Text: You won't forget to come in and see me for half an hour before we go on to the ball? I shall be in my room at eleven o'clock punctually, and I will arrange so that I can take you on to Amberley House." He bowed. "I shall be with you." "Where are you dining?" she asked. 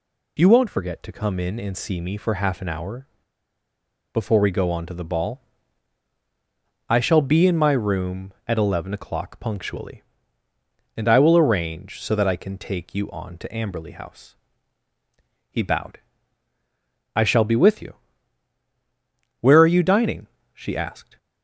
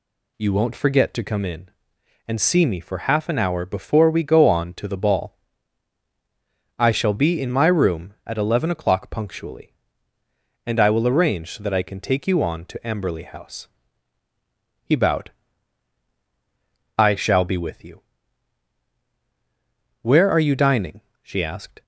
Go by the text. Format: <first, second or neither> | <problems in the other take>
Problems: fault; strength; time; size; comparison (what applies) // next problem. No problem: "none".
second | pauses between "hour" and "before"; at 3.0 s; 1.0 s long